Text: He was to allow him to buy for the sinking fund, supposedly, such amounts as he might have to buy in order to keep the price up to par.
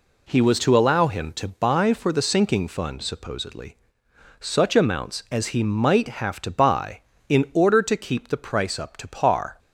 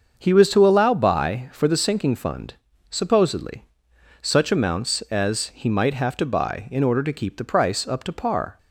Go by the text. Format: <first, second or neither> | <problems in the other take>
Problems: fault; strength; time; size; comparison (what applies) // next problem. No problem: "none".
first | starts louder than the rest; until 1.2 s; 6.5 dB // skips "him to"; at 0.9 s